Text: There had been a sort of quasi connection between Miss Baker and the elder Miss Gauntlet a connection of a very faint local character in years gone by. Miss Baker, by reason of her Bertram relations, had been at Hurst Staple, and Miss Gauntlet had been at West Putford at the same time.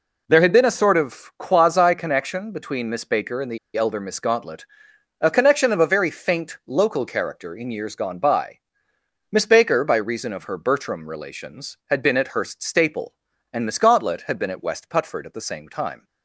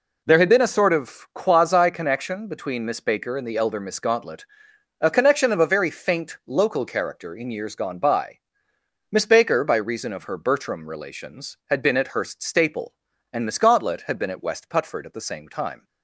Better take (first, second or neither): second